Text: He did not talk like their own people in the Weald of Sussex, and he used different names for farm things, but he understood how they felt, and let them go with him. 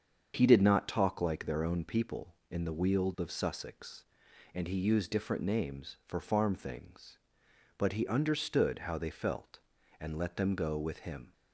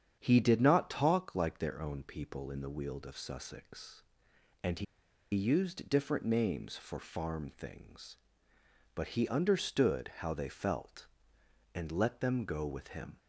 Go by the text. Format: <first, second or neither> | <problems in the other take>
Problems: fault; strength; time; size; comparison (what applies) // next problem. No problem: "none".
first | starts louder than the rest; strong; until 1.2 s; 8.5 dB; strong in the first // pauses between "he" and "used"; noticeable; at 4.8 s; 0.51 s long